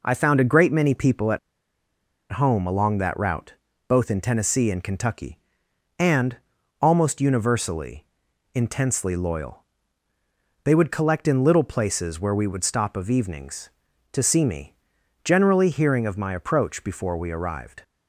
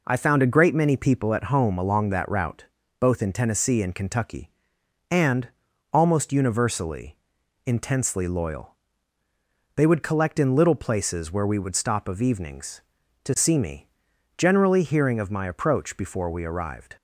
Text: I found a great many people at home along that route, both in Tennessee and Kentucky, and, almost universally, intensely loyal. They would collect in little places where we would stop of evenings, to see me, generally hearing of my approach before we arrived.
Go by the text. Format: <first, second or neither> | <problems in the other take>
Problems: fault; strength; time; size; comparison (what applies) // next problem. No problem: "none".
second | pauses between "at" and "home"; noticeable; at 1.3 s; 0.93 s long